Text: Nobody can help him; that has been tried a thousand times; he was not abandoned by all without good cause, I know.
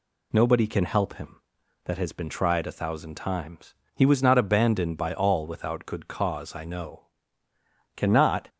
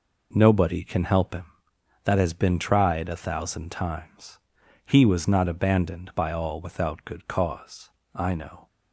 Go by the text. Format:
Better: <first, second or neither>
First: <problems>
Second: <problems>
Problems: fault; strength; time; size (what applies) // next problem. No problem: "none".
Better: second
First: goes on to say "Cannot"; from 7.9 s on; 0.52 s long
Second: none